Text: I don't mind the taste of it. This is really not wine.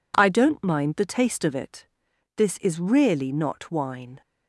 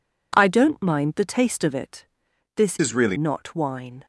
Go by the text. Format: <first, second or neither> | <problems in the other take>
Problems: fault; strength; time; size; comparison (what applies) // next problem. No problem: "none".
first | changes voice from "is" to "really"; from 2.8 to 3.1 s; 0.3 s long